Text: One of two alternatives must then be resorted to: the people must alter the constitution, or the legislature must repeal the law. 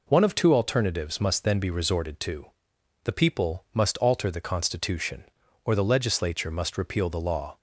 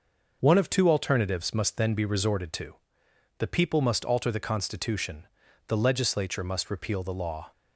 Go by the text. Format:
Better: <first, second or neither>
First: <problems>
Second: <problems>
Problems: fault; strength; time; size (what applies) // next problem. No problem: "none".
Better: first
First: none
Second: skips "or"; at 5.4 s